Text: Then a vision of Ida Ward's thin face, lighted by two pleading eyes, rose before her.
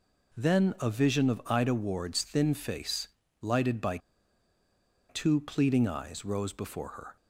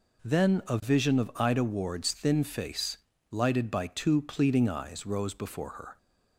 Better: second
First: pauses between "by" and "two"; at 3.9 s; 1.1 s long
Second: none

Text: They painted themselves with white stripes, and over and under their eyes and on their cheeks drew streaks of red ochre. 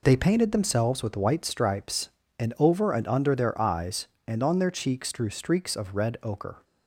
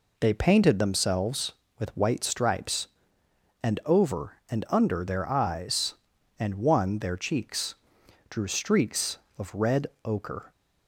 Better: first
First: none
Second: says "one" for "on"; at 6.5 s // pauses between "cheeks" and "drew"; noticeable; at 7.7 s; 0.56 s long // pauses between "red" and "ochre"; slight; at 9.8 s; 0.18 s long

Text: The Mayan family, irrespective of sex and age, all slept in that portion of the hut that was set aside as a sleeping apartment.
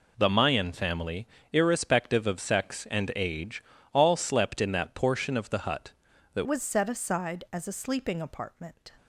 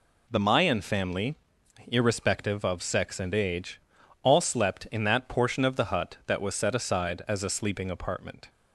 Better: second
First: changes voice at "was"; from 6.4 s on; 2.4 s long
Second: none

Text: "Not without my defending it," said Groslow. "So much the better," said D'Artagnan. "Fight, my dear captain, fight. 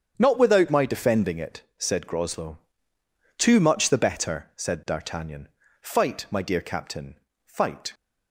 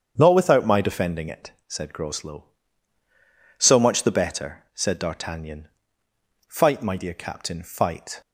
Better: second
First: starts louder than the rest; strong; until 1.1 s; 8 dB // says "Too" for "So"; at 3.3 s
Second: starts louder than the rest; strong; until 1.1 s; 7.5 dB

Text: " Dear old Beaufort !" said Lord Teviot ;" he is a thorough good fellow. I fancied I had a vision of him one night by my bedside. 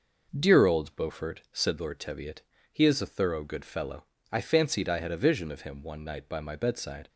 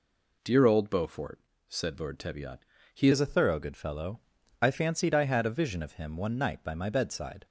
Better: first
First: none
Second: changes voice at "is"; from 3.1 s on; 4.3 s long

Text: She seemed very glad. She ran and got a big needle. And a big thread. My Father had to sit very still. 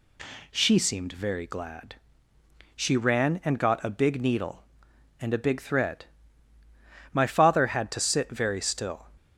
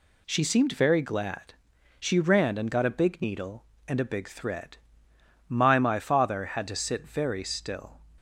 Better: first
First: none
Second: says "My" twice; at 5.7 s

